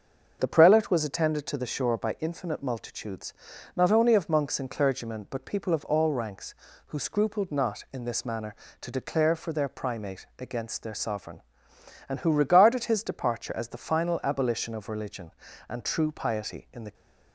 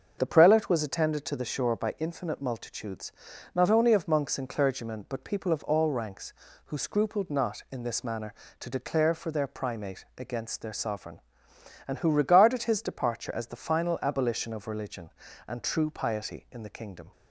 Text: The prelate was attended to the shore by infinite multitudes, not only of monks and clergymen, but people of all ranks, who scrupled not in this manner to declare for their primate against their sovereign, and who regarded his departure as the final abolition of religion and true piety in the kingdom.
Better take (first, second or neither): second